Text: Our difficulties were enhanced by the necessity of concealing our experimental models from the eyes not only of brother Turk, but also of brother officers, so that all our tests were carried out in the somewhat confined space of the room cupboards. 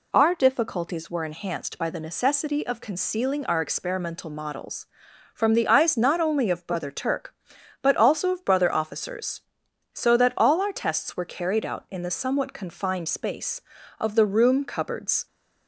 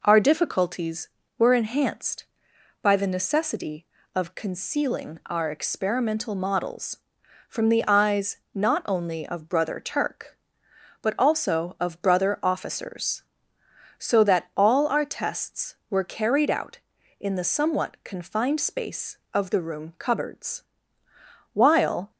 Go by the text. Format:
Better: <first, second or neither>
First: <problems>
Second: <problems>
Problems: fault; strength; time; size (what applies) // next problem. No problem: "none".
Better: first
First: none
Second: pauses between "eyes" and "not"; slight; at 8.3 s; 0.18 s long // goes on to say "While"; from 21.5 s on; 0.58 s long